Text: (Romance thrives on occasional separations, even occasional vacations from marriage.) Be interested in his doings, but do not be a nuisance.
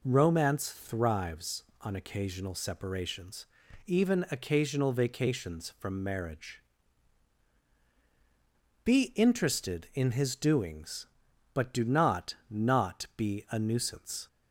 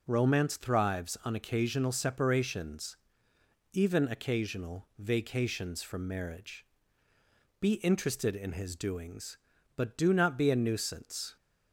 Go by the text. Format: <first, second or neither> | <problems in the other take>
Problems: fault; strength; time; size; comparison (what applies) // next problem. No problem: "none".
second | says "not" twice; at 12.4 s